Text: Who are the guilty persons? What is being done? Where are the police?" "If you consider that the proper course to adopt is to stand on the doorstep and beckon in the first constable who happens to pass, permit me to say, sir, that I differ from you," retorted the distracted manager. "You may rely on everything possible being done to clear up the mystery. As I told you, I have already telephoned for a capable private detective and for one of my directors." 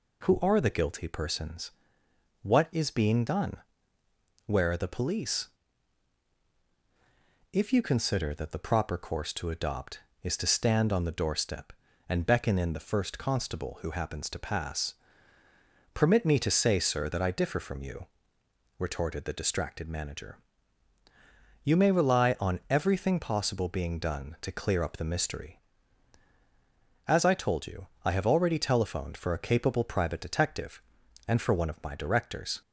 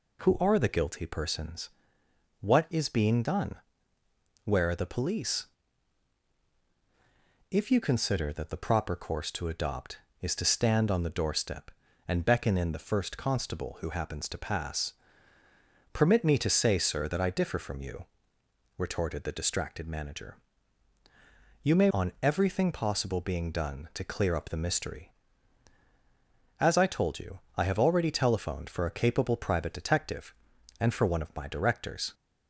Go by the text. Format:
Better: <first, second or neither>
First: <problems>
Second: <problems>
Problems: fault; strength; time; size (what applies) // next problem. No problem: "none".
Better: first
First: none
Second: skips "rely"; at 21.8 s